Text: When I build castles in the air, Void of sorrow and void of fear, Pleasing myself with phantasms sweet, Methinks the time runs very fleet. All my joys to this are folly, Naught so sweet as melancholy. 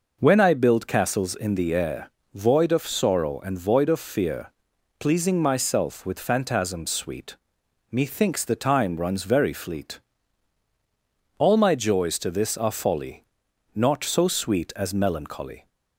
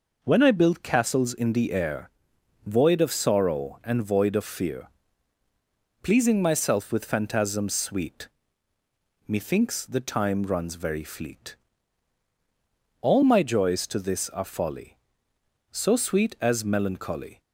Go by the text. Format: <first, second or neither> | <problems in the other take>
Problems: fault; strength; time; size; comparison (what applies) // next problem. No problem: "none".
first | skips "Naught"; at 15.3 s